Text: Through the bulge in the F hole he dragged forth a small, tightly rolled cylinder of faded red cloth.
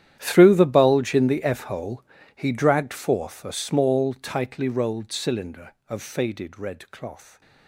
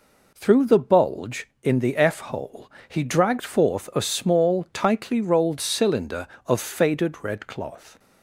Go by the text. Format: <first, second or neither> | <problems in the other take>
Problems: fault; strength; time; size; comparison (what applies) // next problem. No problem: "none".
second | gets quieter; strong; throughout; 19.5 dB // pauses between "hole" and "he"; slight; at 2.0 s; 0.32 s long; slight in the second